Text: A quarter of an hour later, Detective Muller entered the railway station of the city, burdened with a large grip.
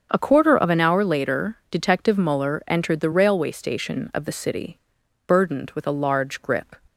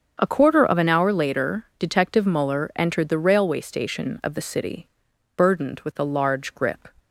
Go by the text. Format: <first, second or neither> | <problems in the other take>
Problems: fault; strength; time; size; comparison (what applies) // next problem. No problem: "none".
neither | starts louder than the rest; the same in both